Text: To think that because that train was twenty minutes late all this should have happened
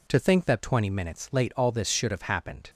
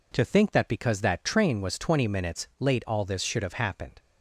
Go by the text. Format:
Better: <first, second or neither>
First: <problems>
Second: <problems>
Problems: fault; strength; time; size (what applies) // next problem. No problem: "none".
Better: second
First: skips "because that train was"; at 0.6 s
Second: none